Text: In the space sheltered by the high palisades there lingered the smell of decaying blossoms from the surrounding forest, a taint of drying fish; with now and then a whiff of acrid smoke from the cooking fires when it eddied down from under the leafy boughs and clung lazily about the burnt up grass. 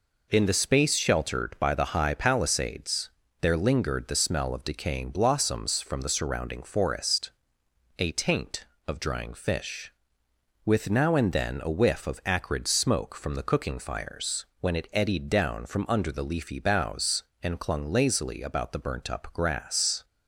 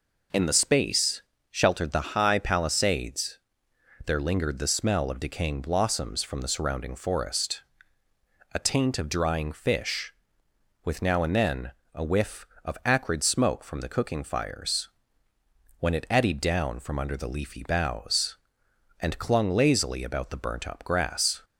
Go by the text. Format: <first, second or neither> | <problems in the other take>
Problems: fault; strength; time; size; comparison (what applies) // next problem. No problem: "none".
first | pauses between "space" and "sheltered"; slight; at 1.2 s; 0.28 s long // skips "by"; at 1.9 s // pauses between "palisades" and "there"; noticeable; at 3.4 s; 0.66 s long; slight in the first // pauses between "then" and "a"; slight; at 11.7 s; 0.22 s long // pauses between "fires" and "when"; noticeable; at 14.8 s; 0.92 s long; slight in the first